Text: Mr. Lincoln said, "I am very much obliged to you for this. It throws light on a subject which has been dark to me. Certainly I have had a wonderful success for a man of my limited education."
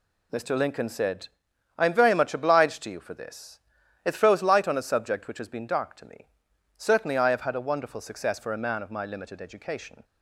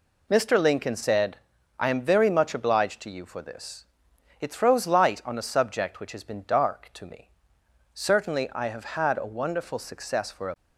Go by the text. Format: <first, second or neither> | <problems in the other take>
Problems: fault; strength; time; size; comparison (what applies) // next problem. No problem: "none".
first | stops before "man of my limited education"; at 10.5 s